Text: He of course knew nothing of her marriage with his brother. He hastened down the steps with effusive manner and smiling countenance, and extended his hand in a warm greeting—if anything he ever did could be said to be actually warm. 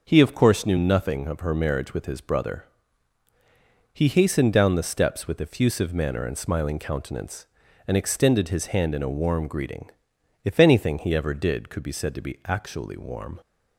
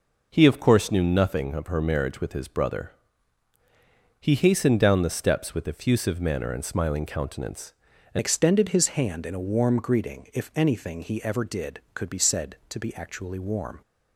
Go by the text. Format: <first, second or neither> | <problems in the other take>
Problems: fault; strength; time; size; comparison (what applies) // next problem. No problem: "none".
first | changes voice at "extended"; from 8.1 s on; 5.7 s long